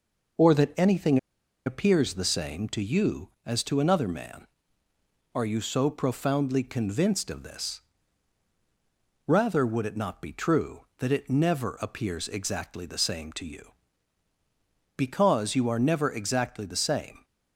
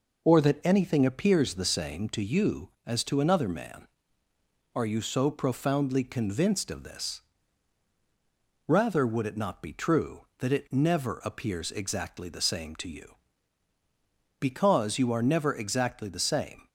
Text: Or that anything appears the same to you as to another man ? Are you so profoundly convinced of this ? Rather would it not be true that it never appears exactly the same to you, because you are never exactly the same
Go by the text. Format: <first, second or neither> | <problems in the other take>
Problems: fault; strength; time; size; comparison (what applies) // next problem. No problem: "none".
second | pauses between "anything" and "appears"; noticeable; at 1.1 s; 0.48 s long